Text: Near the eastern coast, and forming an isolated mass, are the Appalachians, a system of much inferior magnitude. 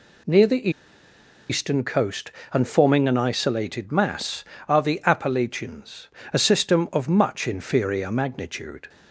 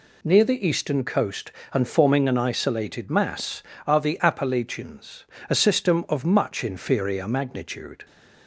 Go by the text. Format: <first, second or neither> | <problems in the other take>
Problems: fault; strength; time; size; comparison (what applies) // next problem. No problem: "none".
second | pauses between "the" and "eastern"; noticeable; at 0.6 s; 0.80 s long